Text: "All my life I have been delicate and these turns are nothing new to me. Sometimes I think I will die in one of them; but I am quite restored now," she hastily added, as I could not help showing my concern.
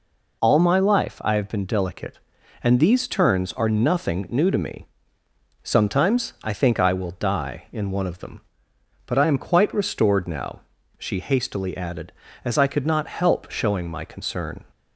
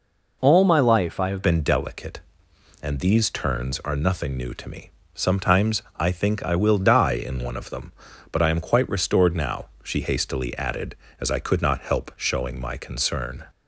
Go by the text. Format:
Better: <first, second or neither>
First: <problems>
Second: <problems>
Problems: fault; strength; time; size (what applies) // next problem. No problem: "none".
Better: first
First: none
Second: changes voice at "been"; from 1.4 s on; 12.0 s long // pauses between "Sometimes" and "I"; slight; at 5.8 s; 0.16 s long